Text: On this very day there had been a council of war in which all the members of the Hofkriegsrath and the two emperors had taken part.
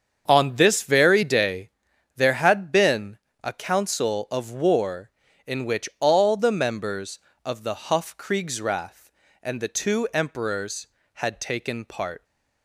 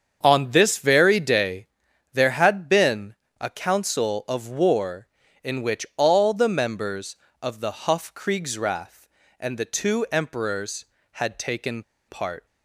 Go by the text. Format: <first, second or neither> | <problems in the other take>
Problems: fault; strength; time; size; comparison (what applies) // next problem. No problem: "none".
first | starts louder than the rest; until 1.2 s; 7 dB; also in the first // pauses between "day" and "there"; noticeable; at 1.6 s; 0.48 s long; noticeable in the first // pauses between "been" and "a"; slight; at 3.1 s; 0.24 s long; slight in the first // pauses between "taken" and "part"; slight; at 11.8 s; 0.26 s long